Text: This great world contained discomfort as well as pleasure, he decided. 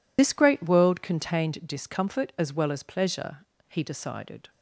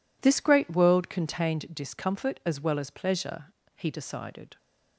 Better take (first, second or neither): second